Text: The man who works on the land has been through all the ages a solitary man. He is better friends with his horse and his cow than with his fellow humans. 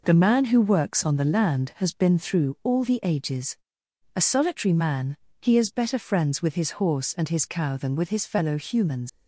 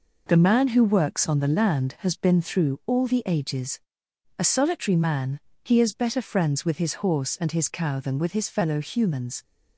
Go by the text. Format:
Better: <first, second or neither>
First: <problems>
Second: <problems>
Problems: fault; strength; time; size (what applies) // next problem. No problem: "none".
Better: second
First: pauses between "ages" and "a"; noticeable; at 3.5 s; 0.58 s long // leaves "humans" unfinished; at 9.0 s; 105 ms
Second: pauses between "ages" and "a"; noticeable; at 3.7 s; 0.58 s long